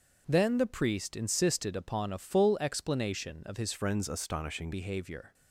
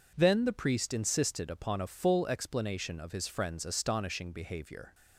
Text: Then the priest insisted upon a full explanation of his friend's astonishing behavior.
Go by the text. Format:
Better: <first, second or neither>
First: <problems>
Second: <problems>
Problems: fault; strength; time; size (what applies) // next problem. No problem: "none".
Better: second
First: starts louder than the rest; until 1.2 s; 6.5 dB // changes voice from "friend's" to "astonishing"; from 3.7 to 4.7 s; 1.0 s long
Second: none